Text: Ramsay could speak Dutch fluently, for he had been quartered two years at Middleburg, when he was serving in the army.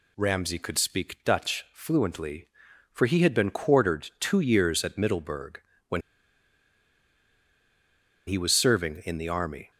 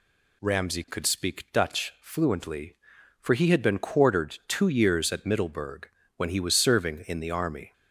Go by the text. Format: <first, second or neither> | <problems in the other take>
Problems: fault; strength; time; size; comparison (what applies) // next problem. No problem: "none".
second | pauses between "when" and "he"; strong; at 6.0 s; 2.2 s long